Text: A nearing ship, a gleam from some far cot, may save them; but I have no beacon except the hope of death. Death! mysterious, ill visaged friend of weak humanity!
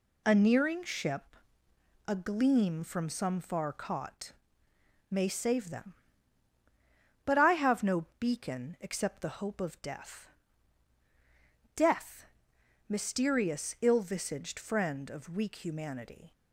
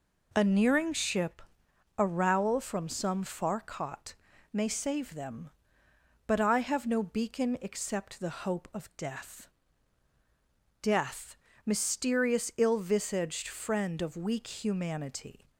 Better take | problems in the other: first | says "rowel" for "gleam"; at 2.0 s

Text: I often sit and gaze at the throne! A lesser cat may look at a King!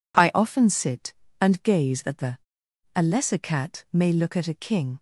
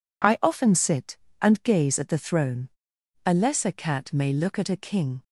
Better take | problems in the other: second | skips "throne"; at 2.6 s

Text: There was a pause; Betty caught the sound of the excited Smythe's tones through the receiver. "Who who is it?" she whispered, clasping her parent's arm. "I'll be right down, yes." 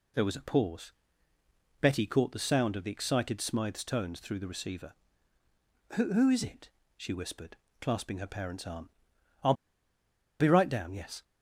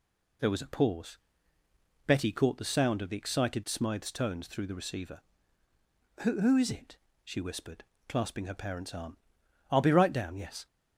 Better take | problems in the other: second | pauses between "I'll" and "be"; noticeable; at 9.5 s; 0.87 s long

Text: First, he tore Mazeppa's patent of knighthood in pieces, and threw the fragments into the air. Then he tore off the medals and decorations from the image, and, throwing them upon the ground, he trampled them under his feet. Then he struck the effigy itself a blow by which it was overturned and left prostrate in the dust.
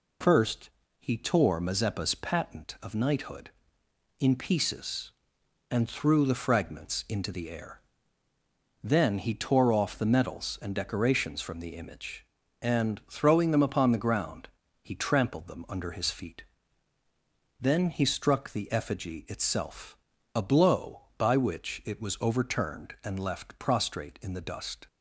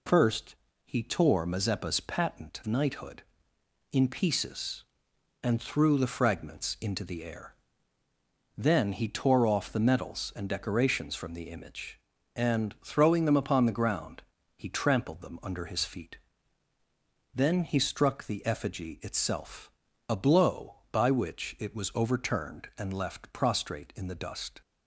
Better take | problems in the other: first | skips "of"; at 2.6 s // pauses between "itself" and "a"; at 19.6 s; 0.40 s long; also in the first

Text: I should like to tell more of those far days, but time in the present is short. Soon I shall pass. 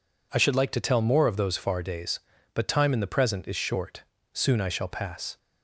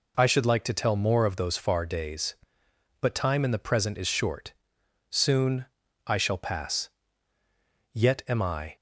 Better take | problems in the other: first | pauses between "Soon" and "I"; at 5.6 s; 0.42 s long // goes on to say "Yet am I"; noticeable; from 7.9 s on; 0.82 s long

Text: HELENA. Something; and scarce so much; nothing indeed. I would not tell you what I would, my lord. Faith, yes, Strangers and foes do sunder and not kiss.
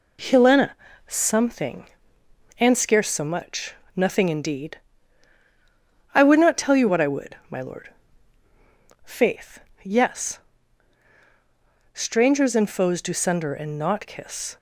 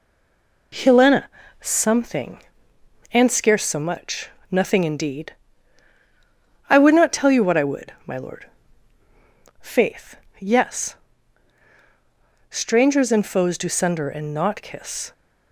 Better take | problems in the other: first | stays silent before the first word; slight; until 0.7 s; 0.7 s long

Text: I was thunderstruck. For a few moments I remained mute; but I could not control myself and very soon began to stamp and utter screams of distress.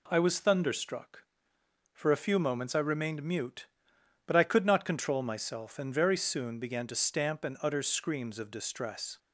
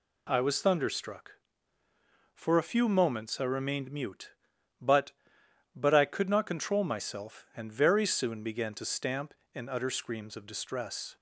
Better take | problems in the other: first | says "but" twice; at 5.7 s

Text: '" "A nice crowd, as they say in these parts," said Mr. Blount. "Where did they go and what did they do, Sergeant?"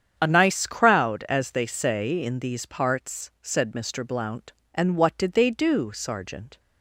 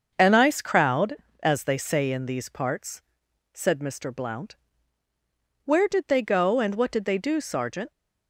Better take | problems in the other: second | starts louder than the rest; strong; until 1.1 s; 8 dB; also in the second // skips "Where did they go"; at 4.6 s

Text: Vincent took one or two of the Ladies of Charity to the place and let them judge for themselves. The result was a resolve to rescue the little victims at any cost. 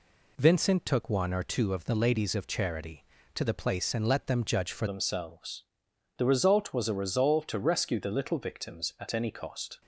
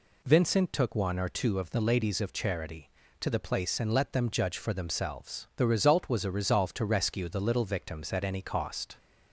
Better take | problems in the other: second | changes voice at "themselves"; from 4.8 s on; 5.0 s long

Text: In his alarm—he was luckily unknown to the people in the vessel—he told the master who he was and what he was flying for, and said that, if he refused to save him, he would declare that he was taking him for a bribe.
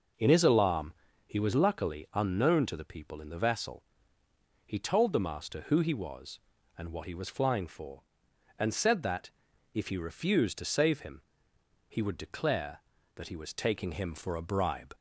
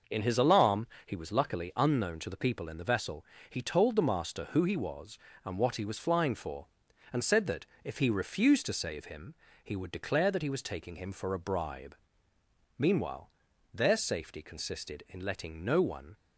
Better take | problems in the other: first | goes on to say "Meanwhile their safety consisted in letting no one"; strong; from 12.7 s on; 3.3 s long

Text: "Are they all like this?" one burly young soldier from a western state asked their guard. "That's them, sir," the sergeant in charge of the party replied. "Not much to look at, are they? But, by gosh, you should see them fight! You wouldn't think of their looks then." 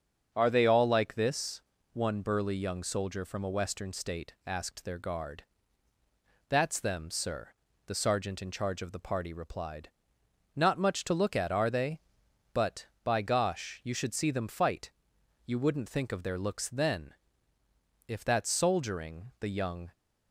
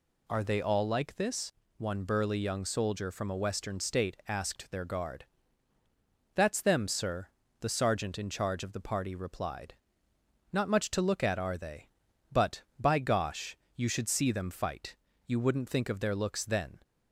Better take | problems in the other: second | starts louder than the rest; until 1.3 s; 7 dB // goes on to say "If that's soldiering the young"; strong; from 18.0 s on; 1.8 s long

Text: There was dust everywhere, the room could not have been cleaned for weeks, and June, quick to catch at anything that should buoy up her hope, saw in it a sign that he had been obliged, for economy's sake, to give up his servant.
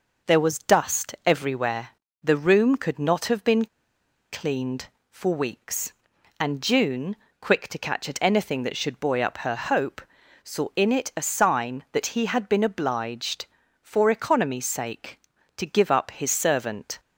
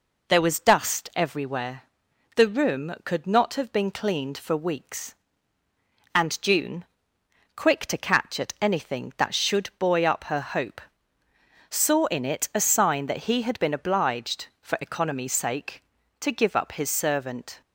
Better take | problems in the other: second | pauses between "been" and "cleaned"; noticeable; at 3.6 s; 0.67 s long

